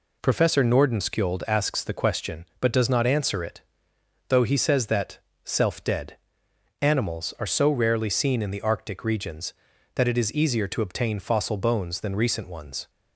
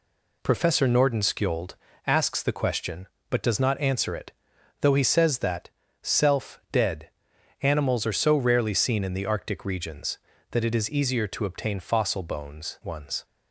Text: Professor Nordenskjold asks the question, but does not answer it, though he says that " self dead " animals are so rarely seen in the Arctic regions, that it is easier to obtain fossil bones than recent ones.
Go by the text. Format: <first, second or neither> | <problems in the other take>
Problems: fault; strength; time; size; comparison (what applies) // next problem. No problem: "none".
first | pauses between "Nordenskjold" and "asks"; slight; at 1.7 s; 0.32 s long // skips "than recent"; at 12.8 s